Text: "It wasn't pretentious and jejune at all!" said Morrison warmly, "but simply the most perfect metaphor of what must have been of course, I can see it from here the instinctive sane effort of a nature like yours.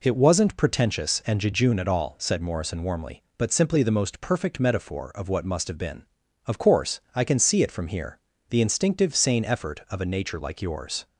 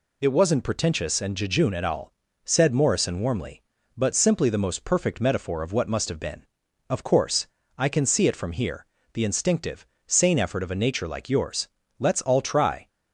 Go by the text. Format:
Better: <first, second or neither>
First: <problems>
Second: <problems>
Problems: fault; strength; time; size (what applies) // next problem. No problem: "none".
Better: first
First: pauses between "here" and "the"; slight; at 8.1 s; 0.30 s long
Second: pauses between "here" and "the"; slight; at 8.8 s; 0.26 s long // pauses between "instinctive" and "sane"; slight; at 9.8 s; 0.22 s long // goes on to say "Let's all try"; noticeable; from 11.9 s on; 0.88 s long